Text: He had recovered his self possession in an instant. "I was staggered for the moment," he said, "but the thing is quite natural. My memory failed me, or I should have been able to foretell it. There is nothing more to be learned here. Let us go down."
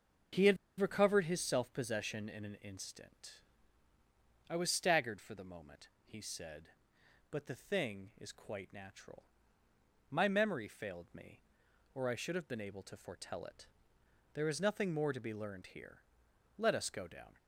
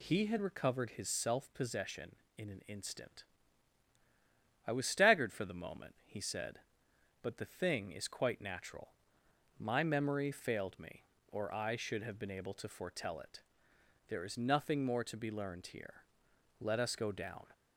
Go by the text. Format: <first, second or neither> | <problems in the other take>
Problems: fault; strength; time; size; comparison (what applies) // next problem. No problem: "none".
second | starts louder than the rest; until 1.5 s; 6.5 dB // pauses between "had" and "recovered"; slight; at 0.5 s; 0.23 s long